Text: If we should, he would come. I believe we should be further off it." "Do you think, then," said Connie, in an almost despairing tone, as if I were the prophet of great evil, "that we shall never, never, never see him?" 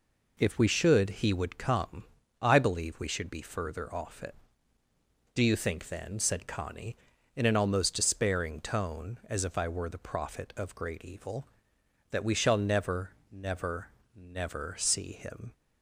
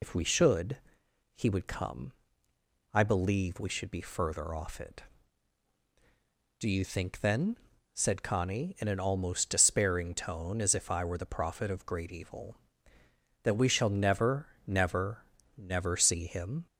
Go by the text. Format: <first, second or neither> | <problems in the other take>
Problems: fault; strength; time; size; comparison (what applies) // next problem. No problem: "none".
first | loses the start of "If"; at 0.0 s; 60 ms